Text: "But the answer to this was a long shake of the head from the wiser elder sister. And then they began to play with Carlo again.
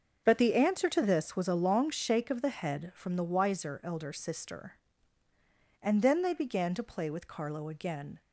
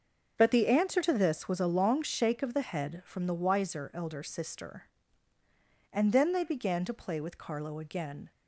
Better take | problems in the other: neither | starts louder than the rest; the same in both

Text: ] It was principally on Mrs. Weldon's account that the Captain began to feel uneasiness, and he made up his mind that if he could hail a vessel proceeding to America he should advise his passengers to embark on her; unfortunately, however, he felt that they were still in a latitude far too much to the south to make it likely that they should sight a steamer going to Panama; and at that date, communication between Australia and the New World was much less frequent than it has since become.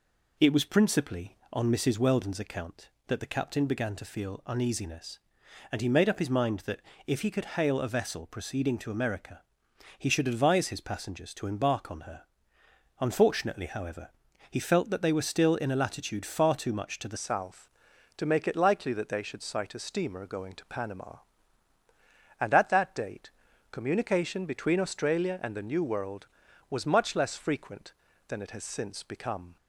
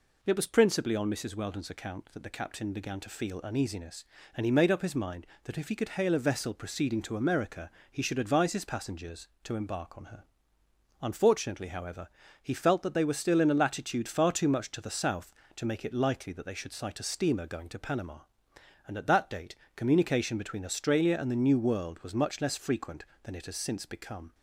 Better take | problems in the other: second | pauses between "that" and "if"; slight; at 6.8 s; 0.26 s long // pauses between "America" and "he"; noticeable; at 9.4 s; 0.56 s long; slight in the second // changes voice at "south"; from 17.1 s on; 12.4 s long

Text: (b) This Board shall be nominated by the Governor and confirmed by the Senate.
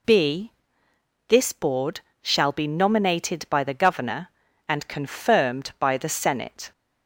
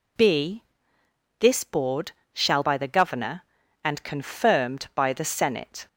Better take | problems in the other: first | pauses between "Board" and "shall"; slight; at 2.1 s; 0.20 s long; slight in the first // skips "be nominated"; at 2.6 s

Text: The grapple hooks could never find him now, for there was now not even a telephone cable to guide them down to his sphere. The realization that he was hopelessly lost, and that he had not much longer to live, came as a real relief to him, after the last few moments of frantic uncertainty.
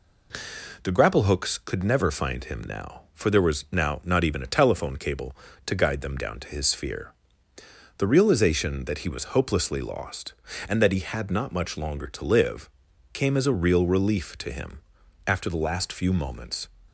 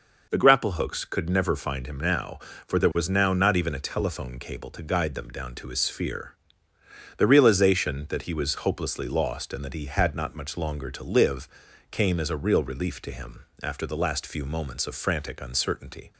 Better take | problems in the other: second | stops before "of frantic uncertainty"; at 16.8 s

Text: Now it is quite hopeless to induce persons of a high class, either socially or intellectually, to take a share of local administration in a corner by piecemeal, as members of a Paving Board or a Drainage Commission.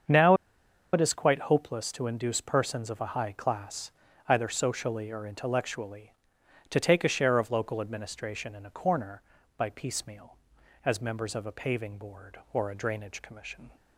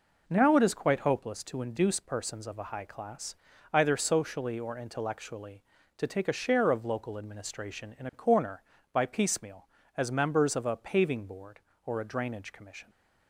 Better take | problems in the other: second | starts louder than the rest; strong; until 1.6 s; 7 dB // pauses between "Now" and "it"; noticeable; at 0.3 s; 0.59 s long

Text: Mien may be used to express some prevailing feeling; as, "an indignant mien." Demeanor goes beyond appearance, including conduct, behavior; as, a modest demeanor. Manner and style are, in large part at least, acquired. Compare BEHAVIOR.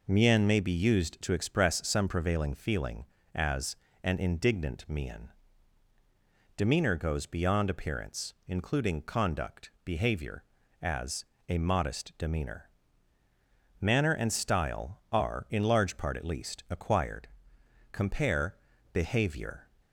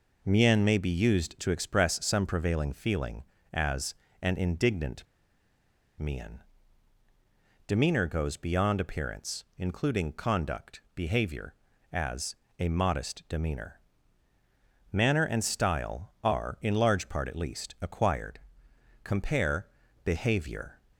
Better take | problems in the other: first | pauses between "indignant" and "mien"; noticeable; at 5.0 s; 0.94 s long // pauses between "Compare" and "BEHAVIOR"; slight; at 19.6 s; 0.36 s long; slight in the first

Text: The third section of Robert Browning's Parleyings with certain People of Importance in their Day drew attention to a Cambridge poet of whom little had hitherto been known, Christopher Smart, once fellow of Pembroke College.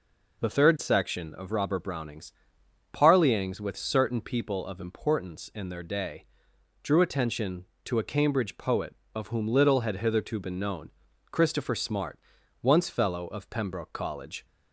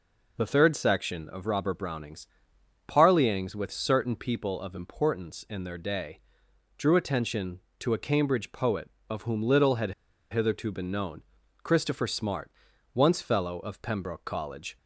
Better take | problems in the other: first | pauses between "Browning's" and "Parleyings"; noticeable; at 2.2 s; 0.62 s long; noticeable in the first // pauses between "Day" and "drew"; noticeable; at 6.1 s; 0.56 s long; noticeable in the first // pauses between "had" and "hitherto"; at 9.9 s; 0.39 s long

